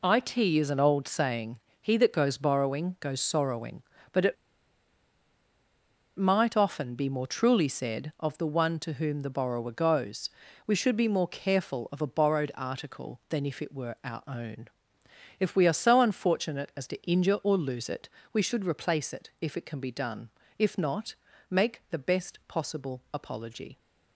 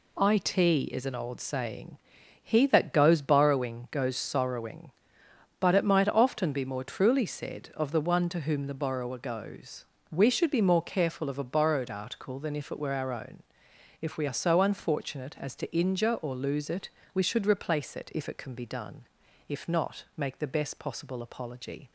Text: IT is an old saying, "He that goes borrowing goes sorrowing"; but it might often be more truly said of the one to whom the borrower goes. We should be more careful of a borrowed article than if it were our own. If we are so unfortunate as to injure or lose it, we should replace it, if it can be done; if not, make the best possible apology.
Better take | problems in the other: second | pauses between "it" and "might"; strong; at 4.3 s; 1.8 s long

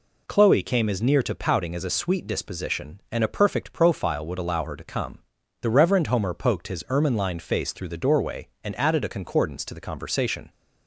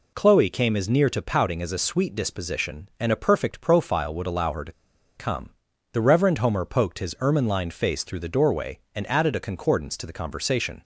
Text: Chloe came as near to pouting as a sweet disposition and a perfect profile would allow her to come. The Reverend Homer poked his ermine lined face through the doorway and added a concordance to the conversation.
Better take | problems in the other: first | pauses between "to" and "come"; at 4.7 s; 0.45 s long

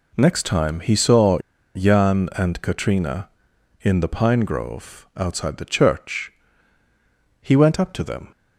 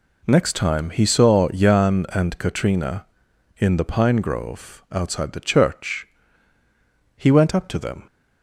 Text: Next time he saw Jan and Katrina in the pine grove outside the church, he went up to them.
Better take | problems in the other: second | pauses between "saw" and "Jan"; slight; at 1.3 s; 0.35 s long

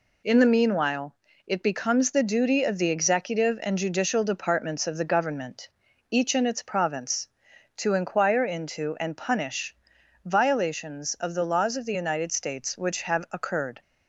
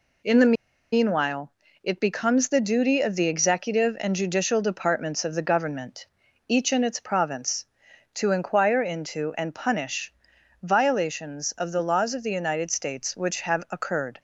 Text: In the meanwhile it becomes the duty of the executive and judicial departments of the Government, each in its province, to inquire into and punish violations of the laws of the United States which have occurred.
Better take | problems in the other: first | pauses between "the" and "meanwhile"; at 0.5 s; 0.39 s long // pauses between "meanwhile" and "it"; slight; at 1.5 s; 0.30 s long; slight in the first // pauses between "punish" and "violations"; noticeable; at 10.1 s; 0.48 s long; noticeable in the first

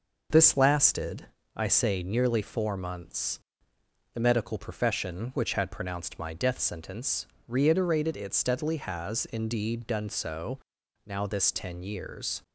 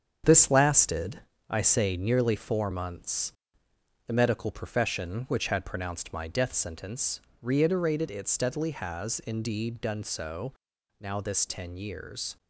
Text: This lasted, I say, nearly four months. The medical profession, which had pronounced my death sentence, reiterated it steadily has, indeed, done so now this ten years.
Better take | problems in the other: first | gets quieter; strong; throughout; 8 dB // pauses between "so" and "now"; at 10.5 s; 0.44 s long; also in the first

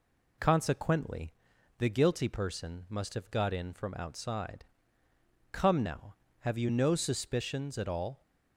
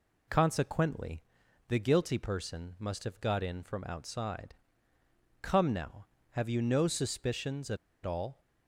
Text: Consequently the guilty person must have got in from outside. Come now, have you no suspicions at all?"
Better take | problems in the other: first | pauses between "Consequently" and "the"; noticeable; at 1.2 s; 0.46 s long; noticeable in the first // pauses between "at" and "all"; slight; at 7.7 s; 0.28 s long

